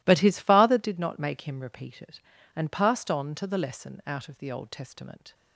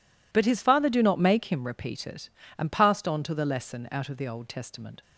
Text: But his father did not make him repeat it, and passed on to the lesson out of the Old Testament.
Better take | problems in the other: first | says "do" for "did"; at 0.8 s

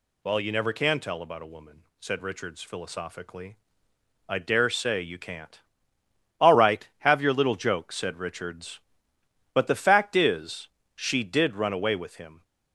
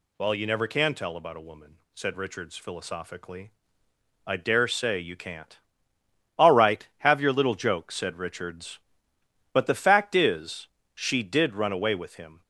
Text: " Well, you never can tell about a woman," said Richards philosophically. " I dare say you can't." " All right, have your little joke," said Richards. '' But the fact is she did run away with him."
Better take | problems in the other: neither | pauses between "is" and "she"; slight; the same in both

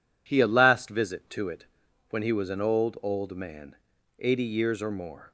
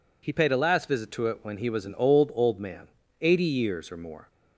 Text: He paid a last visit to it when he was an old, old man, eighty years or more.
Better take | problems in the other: second | skips "paid"; at 0.4 s // pauses between "it" and "when"; at 1.6 s; 0.42 s long

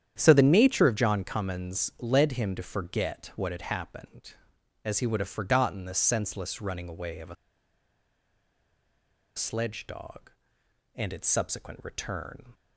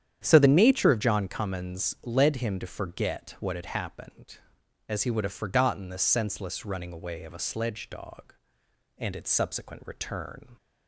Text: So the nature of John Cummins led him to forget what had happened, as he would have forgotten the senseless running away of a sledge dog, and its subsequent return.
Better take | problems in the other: second | starts louder than the rest; strong; until 1.1 s; 9.5 dB; strong in the second // pauses between "a" and "sledge"; strong; at 7.3 s; 2.0 s long

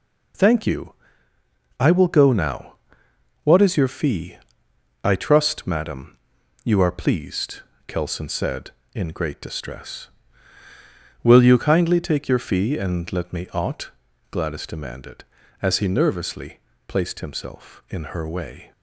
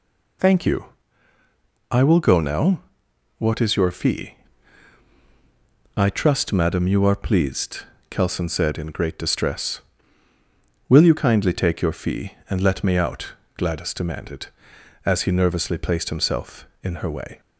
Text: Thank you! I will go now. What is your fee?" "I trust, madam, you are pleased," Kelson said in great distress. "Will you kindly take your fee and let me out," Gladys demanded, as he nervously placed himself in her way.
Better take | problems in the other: second | says "ought" for "out"; at 13.5 s // pauses between "nervously" and "placed"; slight; at 16.5 s; 0.26 s long

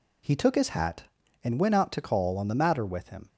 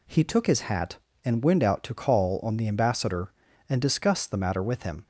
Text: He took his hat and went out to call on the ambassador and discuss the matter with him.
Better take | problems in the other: second | skips "ambassador and discuss the"; at 2.5 s

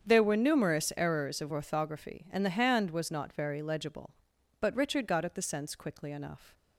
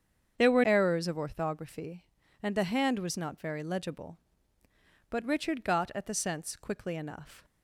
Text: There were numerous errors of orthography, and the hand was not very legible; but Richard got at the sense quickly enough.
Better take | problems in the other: first | starts louder than the rest; strong; until 1.3 s; 8 dB; strong in the first // skips "numerous"; at 0.6 s

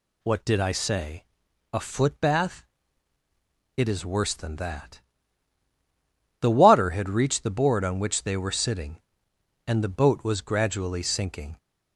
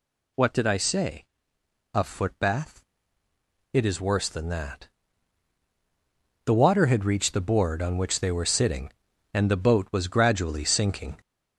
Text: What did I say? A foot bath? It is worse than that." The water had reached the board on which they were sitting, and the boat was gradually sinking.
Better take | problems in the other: first | gets louder; noticeable; throughout; 4.5 dB

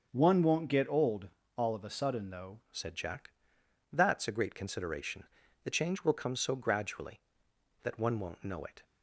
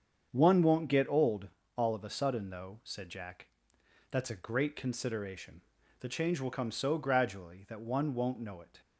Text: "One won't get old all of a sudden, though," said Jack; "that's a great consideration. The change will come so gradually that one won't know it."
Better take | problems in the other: second | starts louder than the rest; until 1.1 s; 6.5 dB; strong in the second // pauses between "old" and "all"; slight; at 1.2 s; 0.28 s long; slight in the second // changes voice at "said"; from 2.7 s on; 6.1 s long

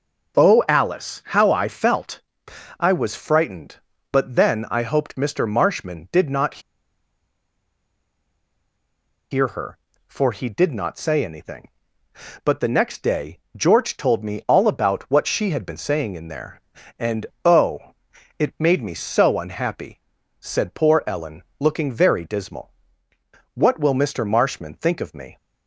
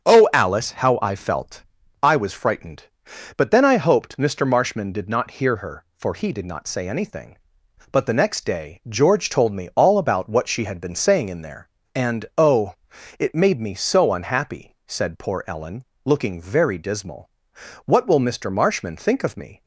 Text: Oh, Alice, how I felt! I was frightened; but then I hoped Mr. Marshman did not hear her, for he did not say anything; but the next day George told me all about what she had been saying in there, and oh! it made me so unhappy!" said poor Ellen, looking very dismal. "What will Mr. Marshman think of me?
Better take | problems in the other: second | starts louder than the rest; until 1.4 s; 6 dB; strong in the second // pauses between "not" and "hear"; strong; at 6.5 s; 2.7 s long // pauses between "day" and "George"; slight; at 13.3 s; 0.20 s long // pauses between "and" and "oh"; slight; at 17.2 s; 0.18 s long

